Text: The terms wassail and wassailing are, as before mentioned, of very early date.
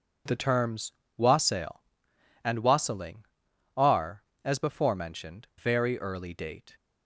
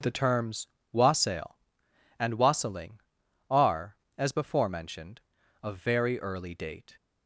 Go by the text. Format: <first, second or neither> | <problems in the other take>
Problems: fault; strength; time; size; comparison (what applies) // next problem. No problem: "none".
second | pauses between "terms" and "wassail"; slight; at 0.9 s; 0.26 s long; slight in the second // skips "of"; at 5.5 s